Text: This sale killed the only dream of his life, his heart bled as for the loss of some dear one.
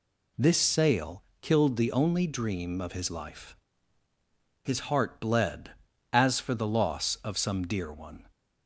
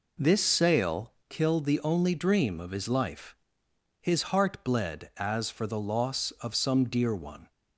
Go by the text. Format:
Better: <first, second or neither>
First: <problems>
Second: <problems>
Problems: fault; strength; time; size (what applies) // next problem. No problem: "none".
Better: neither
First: pauses between "sale" and "killed"; slight; at 1.2 s; 0.20 s long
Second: pauses between "sale" and "killed"; slight; at 1.1 s; 0.16 s long